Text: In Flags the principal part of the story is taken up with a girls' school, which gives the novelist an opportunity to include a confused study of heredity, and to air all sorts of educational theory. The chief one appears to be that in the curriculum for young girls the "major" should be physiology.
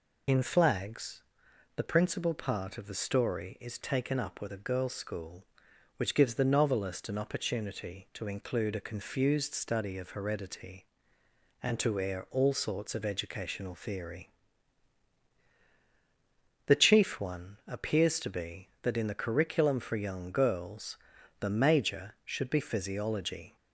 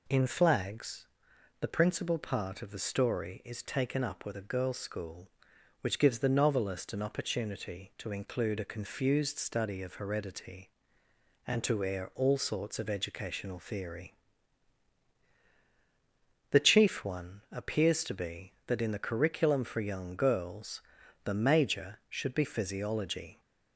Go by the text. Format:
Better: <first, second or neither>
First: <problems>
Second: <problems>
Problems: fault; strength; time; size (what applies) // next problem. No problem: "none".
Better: second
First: loses the start of "In"; at 0.2 s; 45 ms // pauses between "Flags" and "the"; noticeable; at 1.2 s; 0.52 s long // pauses between "girls" and "the"; at 20.9 s; 0.42 s long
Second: pauses between "Flags" and "the"; noticeable; at 1.0 s; 0.52 s long // pauses between "girls" and "the"; at 20.8 s; 0.42 s long